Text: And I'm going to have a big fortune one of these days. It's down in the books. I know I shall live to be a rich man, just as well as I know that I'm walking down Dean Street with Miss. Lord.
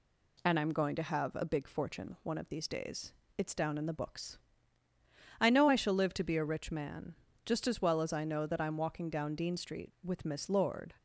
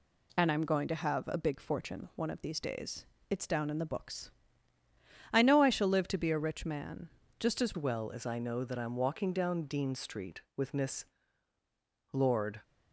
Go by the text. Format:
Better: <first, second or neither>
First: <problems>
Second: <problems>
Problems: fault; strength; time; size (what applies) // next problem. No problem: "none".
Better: first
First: none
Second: changes voice at "well"; from 7.7 s on; 4.9 s long